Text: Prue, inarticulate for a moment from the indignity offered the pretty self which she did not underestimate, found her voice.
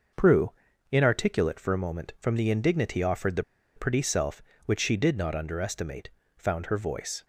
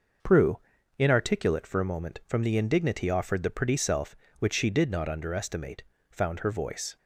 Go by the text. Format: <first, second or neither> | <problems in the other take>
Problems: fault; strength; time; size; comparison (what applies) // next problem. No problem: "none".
second | pauses between "the" and "pretty"; slight; at 3.4 s; 0.33 s long